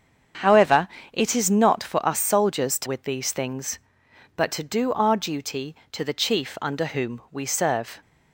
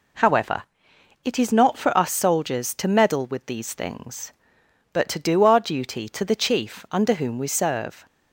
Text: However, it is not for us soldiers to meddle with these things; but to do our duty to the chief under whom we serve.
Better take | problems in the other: second | starts louder than the rest; strong; until 1.6 s; 7.5 dB // skips "meddle"; at 2.8 s

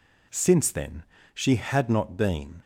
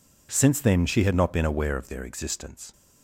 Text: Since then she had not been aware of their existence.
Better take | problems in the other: second | pauses between "then" and "she"; slight; at 1.0 s; 0.30 s long // stops before "aware of their existence"; at 2.6 s

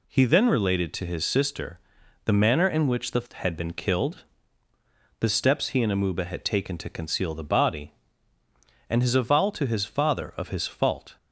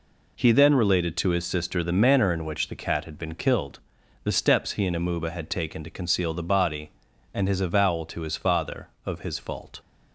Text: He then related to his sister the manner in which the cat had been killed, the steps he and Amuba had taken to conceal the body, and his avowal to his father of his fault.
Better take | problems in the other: second | pauses between "sister" and "the"; noticeable; at 1.7 s; 0.46 s long // skips "cat"; at 3.3 s

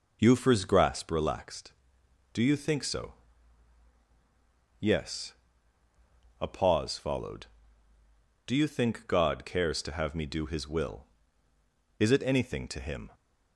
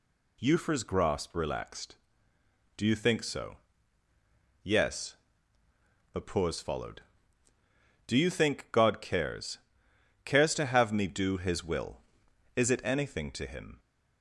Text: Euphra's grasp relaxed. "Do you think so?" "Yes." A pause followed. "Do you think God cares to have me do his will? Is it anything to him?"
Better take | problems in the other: first | says "cares" twice; at 10.2 s

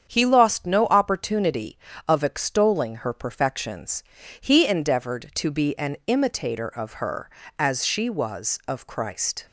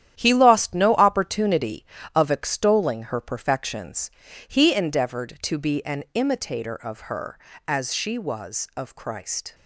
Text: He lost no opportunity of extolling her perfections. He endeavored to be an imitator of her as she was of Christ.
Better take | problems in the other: first | gets quieter; strong; throughout; 9 dB // starts louder than the rest; strong; until 1.2 s; 10.5 dB; strong in the first

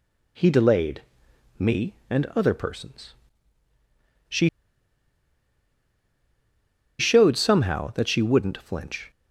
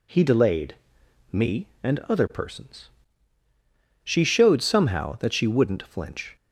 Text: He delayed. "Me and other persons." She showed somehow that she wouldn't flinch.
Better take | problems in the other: second | pauses between "She" and "showed"; strong; at 4.4 s; 2.5 s long

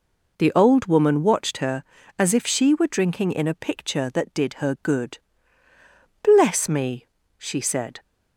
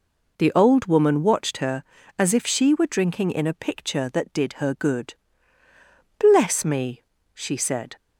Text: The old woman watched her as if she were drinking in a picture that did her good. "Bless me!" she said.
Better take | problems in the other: neither | none

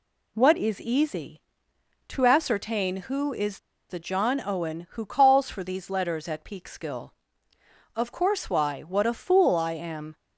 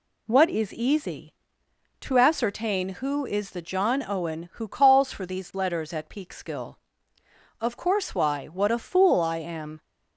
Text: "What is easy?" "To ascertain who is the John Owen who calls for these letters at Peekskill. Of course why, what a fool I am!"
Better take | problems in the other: second | pauses between "is" and "the"; slight; at 3.5 s; 0.31 s long

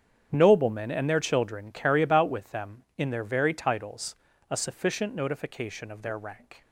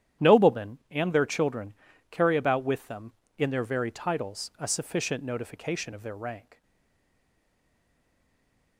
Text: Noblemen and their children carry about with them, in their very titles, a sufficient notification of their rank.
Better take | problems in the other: first | starts louder than the rest; strong; until 1.3 s; 10.5 dB; strong in the first // pauses between "children" and "carry"; slight; at 1.7 s; 0.36 s long // stays silent after the last word; from 6.6 s on; 2.1 s long

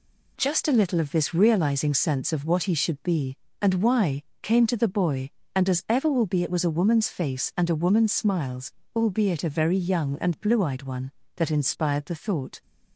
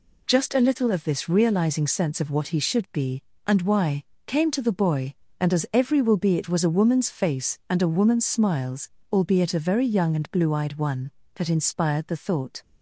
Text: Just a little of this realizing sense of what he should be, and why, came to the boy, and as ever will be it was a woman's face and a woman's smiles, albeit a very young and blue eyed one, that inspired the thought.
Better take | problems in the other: first | says "every" for "ever"; at 5.7 s

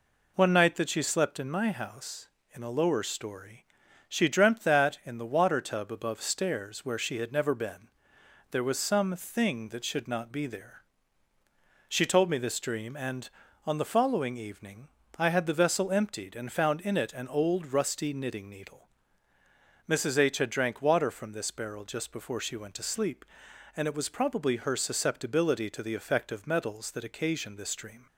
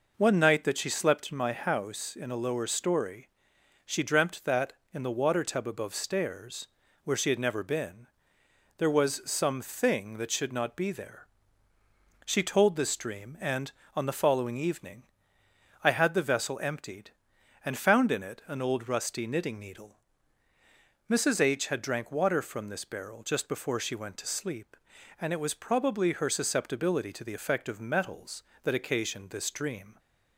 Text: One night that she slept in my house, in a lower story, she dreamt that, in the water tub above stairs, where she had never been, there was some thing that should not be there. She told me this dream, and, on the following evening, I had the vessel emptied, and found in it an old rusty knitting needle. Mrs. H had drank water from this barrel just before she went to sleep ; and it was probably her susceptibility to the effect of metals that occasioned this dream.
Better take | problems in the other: first | skips "me"; at 12.7 s

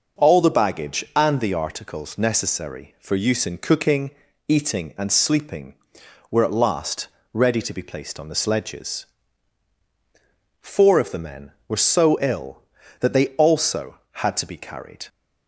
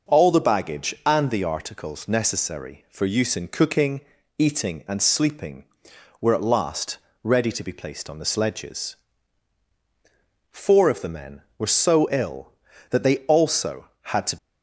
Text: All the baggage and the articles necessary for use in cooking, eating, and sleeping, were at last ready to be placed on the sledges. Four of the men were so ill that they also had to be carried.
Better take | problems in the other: first | pauses between "last" and "ready"; slight; at 6.9 s; 0.26 s long; slight in the first // stops before "be carried"; at 14.3 s

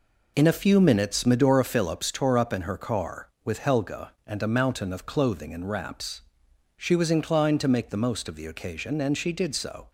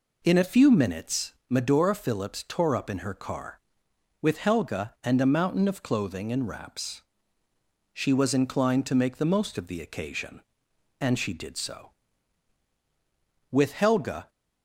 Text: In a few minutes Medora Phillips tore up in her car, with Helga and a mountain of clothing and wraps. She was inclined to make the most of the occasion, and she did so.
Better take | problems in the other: first | pauses between "minutes" and "Medora"; slight; at 1.3 s; 0.16 s long // goes on to say "With Helga"; noticeable; from 13.4 s on; 0.80 s long

